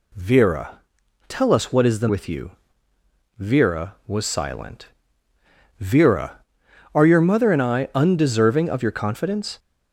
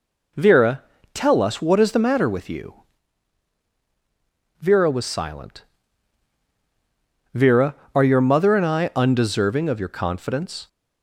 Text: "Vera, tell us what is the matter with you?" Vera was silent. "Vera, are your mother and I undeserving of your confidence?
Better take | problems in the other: second | skips "matter"; at 2.0 s

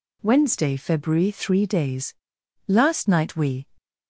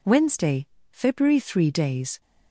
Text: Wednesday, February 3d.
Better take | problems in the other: second | goes on to say "Last night we"; noticeable; from 2.6 s on; 0.98 s long

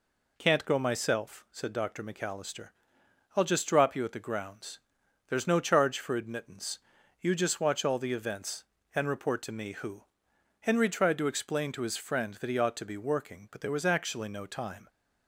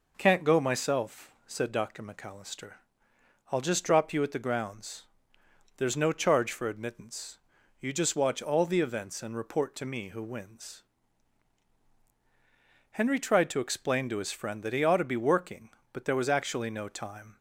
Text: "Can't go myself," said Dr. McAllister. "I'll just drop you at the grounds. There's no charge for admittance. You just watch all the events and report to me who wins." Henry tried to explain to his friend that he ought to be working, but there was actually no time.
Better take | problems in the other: second | skips "wins"; at 10.3 s

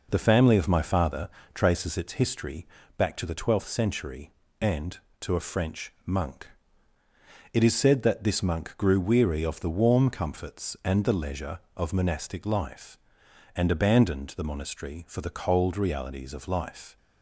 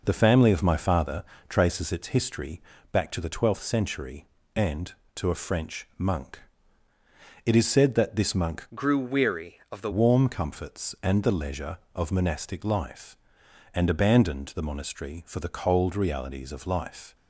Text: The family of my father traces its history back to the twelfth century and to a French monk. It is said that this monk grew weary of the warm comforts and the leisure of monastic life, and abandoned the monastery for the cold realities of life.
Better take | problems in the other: first | pauses between "father" and "traces"; slight; at 1.2 s; 0.24 s long; slight in the first // pauses between "history" and "back"; slight; at 2.6 s; 0.32 s long; slight in the first // changes voice from "grew" to "the"; from 8.7 to 9.9 s; 1.2 s long

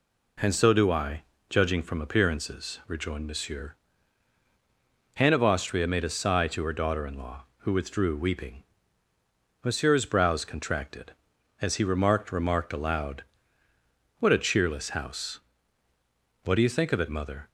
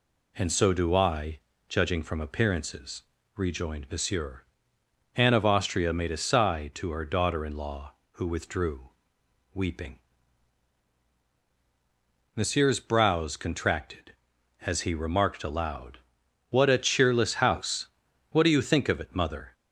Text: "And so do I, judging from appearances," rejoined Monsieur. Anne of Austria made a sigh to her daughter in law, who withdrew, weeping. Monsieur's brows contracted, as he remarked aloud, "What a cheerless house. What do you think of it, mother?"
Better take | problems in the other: second | says "remarked" twice; at 12.3 s

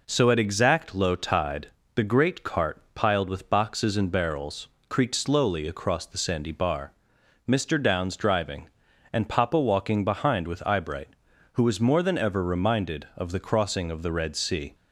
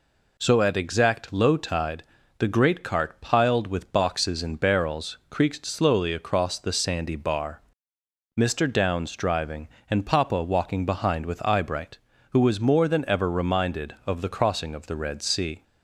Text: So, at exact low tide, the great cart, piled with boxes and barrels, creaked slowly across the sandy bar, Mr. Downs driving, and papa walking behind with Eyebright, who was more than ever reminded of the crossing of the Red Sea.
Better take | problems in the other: neither | none

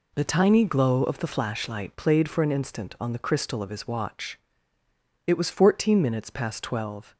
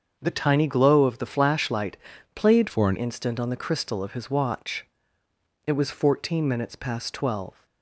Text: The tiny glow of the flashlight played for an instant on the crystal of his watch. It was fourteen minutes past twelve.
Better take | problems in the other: first | starts louder than the rest; until 1.2 s; 6.5 dB // pauses between "flashlight" and "played"; at 1.9 s; 0.38 s long // changes voice from "for" to "an"; from 2.6 to 2.9 s; 0.3 s long

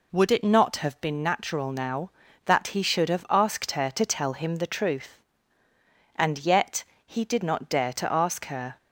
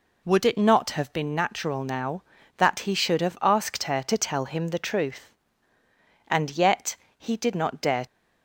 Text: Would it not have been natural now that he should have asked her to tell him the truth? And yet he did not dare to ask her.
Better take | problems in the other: first | pauses between "yet" and "he"; slight; at 6.9 s; 0.22 s long; slight in the first // stops before "to ask her"; at 8.0 s

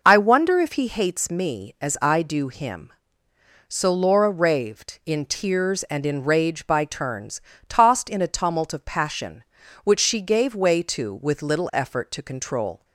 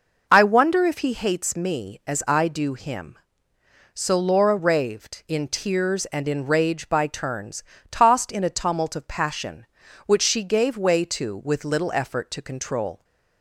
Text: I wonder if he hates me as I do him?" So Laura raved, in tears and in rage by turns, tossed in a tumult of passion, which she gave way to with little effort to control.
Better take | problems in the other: neither | none

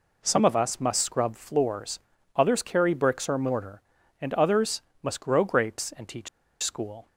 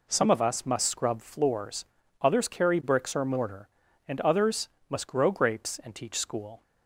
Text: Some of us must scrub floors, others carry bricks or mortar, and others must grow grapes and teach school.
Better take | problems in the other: second | pauses between "others" and "must"; slight; at 4.8 s; 0.20 s long; slight in the second // pauses between "teach" and "school"; slight; at 6.2 s; 0.34 s long

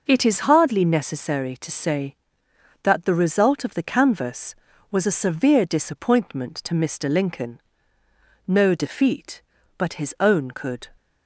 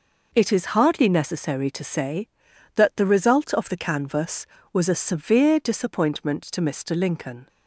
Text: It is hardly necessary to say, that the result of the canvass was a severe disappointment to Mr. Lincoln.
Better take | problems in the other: second | goes on to say "No defeat but his own could"; strong; from 8.4 s on; 2.4 s long

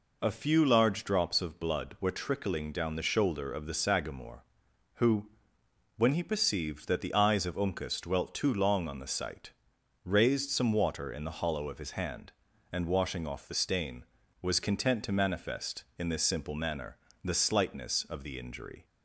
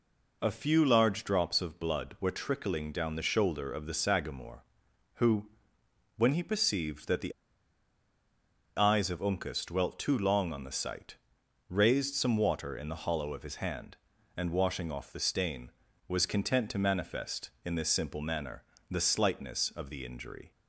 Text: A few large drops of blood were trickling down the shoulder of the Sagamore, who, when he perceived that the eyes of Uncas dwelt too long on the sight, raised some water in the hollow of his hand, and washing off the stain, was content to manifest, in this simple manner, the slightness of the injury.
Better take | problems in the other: first | pauses between "the" and "eyes"; strong; at 7.3 s; 1.4 s long

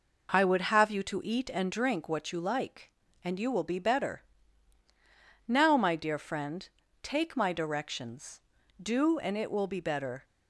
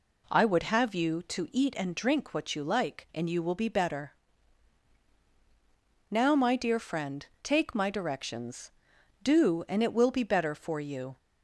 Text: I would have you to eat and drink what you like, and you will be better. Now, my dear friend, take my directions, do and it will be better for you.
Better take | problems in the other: second | stops before "for you"; at 10.2 s

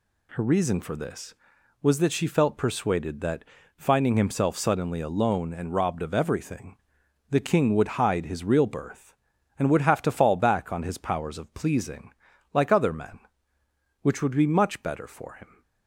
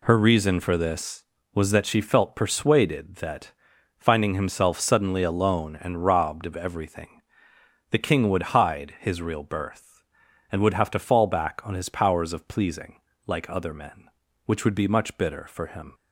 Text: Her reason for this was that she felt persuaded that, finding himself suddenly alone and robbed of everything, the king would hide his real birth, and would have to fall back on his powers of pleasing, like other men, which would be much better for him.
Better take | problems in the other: first | says "bitter" for "better"; at 15.1 s

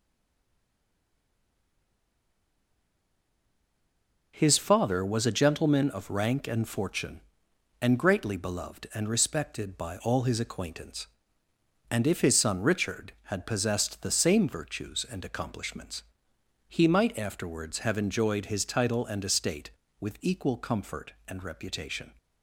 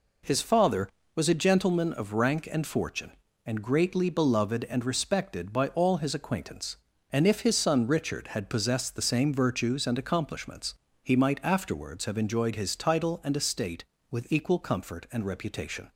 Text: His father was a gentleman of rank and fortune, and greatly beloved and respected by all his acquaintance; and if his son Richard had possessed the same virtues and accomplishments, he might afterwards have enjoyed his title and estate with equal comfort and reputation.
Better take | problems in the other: second | stays silent before the first word; strong; until 4.3 s; 4.3 s long

